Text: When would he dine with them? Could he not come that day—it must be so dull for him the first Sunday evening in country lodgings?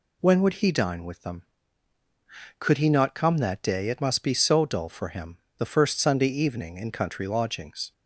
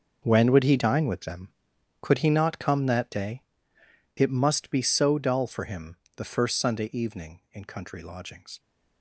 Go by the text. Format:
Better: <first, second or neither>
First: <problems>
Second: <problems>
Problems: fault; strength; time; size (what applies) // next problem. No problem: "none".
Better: first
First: pauses between "him" and "the"; slight; at 5.3 s; 0.20 s long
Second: gets quieter; strong; throughout; 13.5 dB // pauses between "him" and "the"; slight; at 5.9 s; 0.18 s long